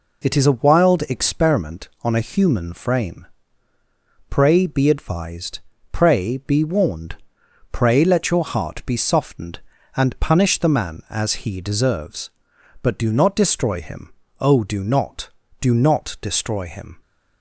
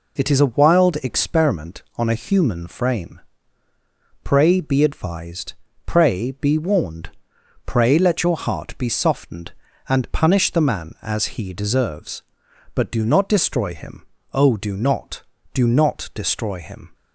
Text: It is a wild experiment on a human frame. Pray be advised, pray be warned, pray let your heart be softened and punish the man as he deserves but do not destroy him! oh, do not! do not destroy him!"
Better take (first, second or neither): neither